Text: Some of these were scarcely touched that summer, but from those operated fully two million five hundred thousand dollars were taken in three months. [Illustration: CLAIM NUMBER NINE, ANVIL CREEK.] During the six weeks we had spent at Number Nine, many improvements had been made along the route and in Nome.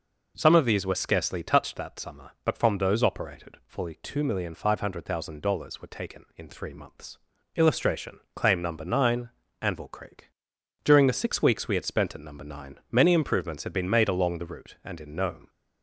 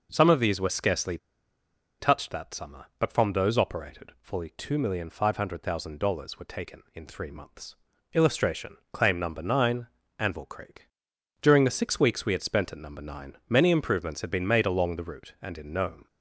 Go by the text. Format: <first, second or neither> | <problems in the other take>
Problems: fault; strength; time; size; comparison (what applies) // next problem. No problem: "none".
first | pauses between "scarcely" and "touched"; noticeable; at 1.1 s; 0.83 s long